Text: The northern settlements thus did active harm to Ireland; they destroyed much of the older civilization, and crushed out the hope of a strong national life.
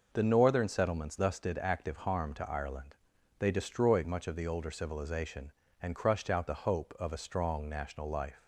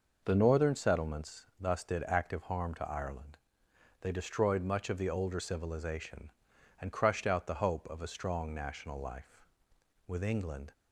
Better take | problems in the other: first | goes on to say "With England"; noticeable; from 10.0 s on; 0.66 s long

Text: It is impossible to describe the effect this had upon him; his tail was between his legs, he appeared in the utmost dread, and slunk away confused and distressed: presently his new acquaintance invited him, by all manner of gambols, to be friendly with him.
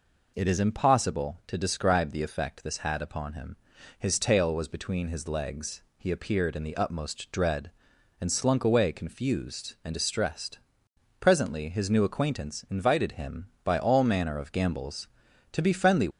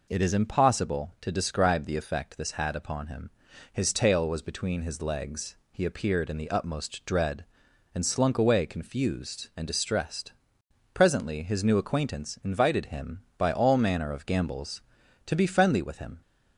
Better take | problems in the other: second | stops before "with him"; at 16.1 s

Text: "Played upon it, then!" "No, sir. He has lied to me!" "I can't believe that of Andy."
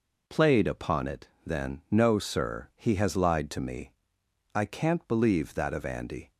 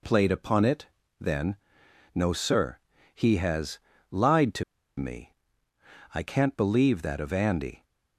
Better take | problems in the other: first | pauses between "has" and "lied"; slight; at 3.7 s; 0.32 s long // pauses between "to" and "me"; at 4.6 s; 0.36 s long

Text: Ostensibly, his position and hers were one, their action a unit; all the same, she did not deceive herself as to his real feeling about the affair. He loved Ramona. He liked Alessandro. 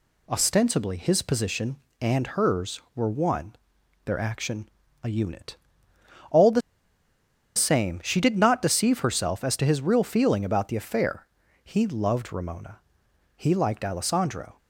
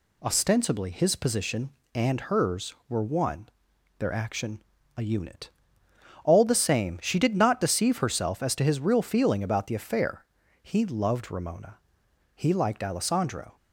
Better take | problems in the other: second | pauses between "action" and "a"; slight; at 4.6 s; 0.36 s long; slight in the second // pauses between "the" and "same"; noticeable; at 6.6 s; 0.96 s long

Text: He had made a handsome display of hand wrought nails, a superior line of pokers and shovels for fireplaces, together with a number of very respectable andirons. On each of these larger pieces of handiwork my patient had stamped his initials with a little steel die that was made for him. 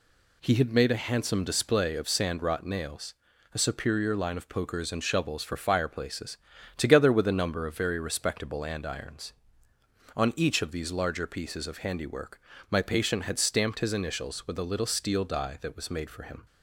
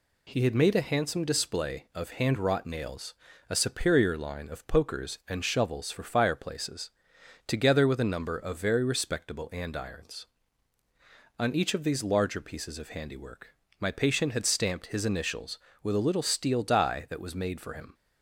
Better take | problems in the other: second | says "sand" for "hand"; at 2.0 s // pauses between "handiwork" and "my"; slight; at 12.4 s; 0.30 s long; slight in the second

